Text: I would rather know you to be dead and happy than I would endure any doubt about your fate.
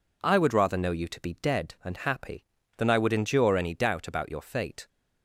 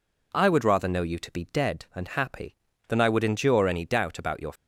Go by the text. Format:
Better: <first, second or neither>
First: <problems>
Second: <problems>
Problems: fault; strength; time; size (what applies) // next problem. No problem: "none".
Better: first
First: none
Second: stops before "fate"; at 4.5 s